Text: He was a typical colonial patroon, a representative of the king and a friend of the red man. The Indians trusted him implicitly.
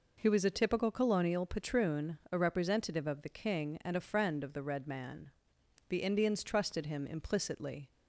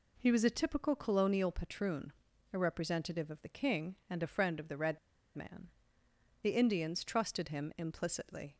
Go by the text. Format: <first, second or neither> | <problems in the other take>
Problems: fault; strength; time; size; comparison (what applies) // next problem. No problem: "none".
first | pauses between "red" and "man"; at 4.9 s; 0.36 s long